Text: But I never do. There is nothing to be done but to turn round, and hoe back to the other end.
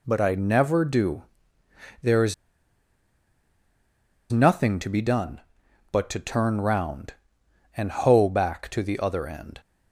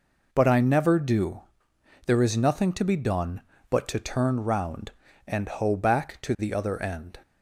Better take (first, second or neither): second